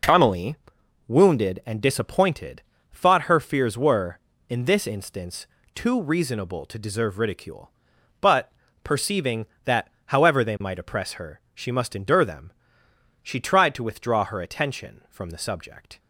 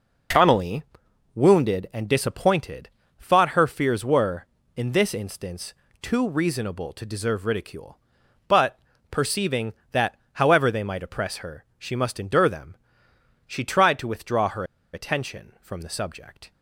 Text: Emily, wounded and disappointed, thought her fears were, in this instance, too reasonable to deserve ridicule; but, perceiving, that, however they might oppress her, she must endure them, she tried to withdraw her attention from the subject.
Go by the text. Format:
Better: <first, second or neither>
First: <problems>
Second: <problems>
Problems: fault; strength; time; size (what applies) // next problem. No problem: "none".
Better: first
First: none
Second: pauses between "her" and "attention"; slight; at 14.6 s; 0.30 s long